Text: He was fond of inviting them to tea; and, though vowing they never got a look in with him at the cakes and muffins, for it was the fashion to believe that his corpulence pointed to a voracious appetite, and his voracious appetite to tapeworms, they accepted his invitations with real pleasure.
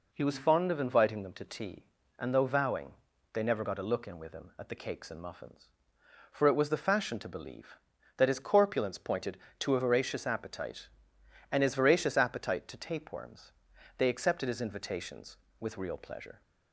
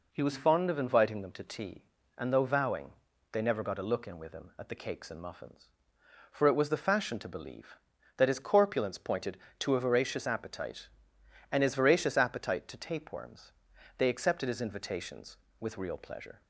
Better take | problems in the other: neither | pauses between "vowing" and "they"; slight; the same in both

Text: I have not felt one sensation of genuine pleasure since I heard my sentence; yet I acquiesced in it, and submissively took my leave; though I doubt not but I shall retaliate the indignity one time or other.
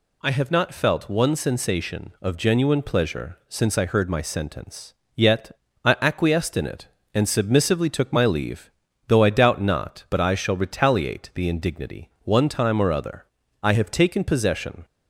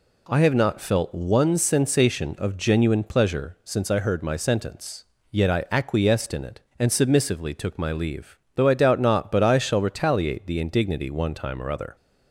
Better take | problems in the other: second | pauses between "yet" and "I"; slight; at 5.5 s; 0.34 s long // pauses between "indignity" and "one"; slight; at 12.0 s; 0.16 s long // goes on to say "I have taken possession"; noticeable; from 13.6 s on; 1.2 s long

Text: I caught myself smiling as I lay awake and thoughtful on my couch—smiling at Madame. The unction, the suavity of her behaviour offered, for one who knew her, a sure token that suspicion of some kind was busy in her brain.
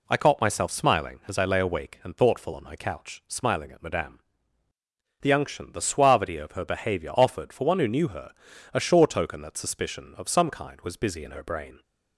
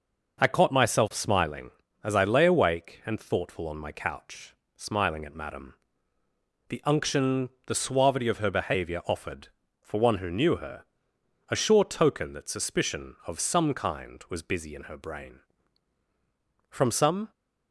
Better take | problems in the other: first | goes on to say "From some"; from 16.7 s on; 0.60 s long

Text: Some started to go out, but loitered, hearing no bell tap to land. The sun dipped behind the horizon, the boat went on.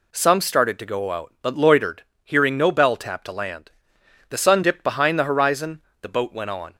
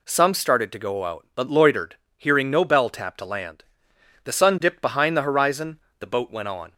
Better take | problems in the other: neither | none

